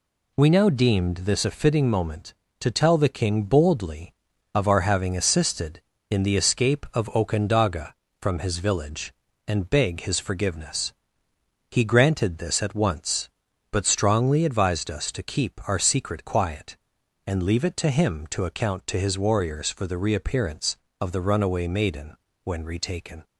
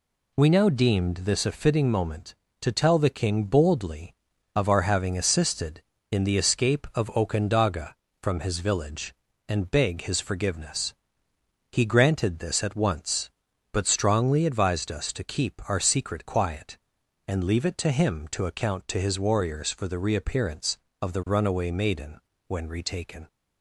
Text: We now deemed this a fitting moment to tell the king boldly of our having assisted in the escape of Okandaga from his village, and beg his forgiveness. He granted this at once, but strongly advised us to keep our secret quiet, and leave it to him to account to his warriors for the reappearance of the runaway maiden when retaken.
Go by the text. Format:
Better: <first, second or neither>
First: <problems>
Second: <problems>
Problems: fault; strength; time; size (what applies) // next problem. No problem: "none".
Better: neither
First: pauses between "maiden" and "when"; slight; at 22.1 s; 0.28 s long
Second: pauses between "maiden" and "when"; slight; at 22.1 s; 0.28 s long